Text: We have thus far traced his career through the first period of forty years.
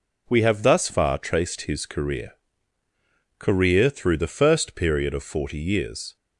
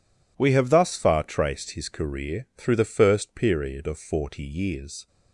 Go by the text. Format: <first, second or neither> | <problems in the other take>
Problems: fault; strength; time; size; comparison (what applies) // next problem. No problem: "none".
second | says "career" twice; at 3.3 s